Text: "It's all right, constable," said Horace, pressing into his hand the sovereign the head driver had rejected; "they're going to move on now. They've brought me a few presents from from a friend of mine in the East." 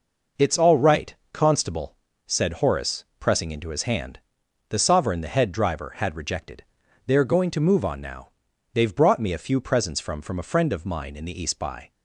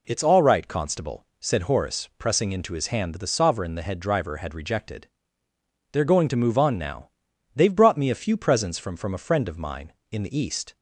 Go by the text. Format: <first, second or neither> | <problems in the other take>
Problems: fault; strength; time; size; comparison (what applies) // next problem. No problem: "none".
second | pauses between "hand" and "the"; noticeable; at 4.1 s; 0.50 s long // goes on to say "By"; slight; from 11.5 s on; 0.34 s long